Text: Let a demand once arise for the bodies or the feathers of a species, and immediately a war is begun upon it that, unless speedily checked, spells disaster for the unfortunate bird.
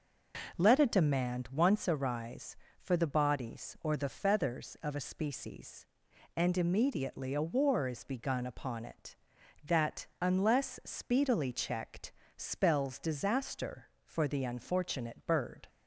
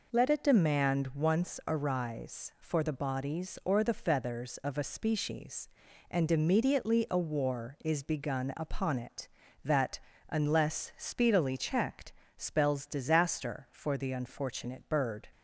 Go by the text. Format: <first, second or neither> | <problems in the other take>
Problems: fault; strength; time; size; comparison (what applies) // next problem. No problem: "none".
neither | none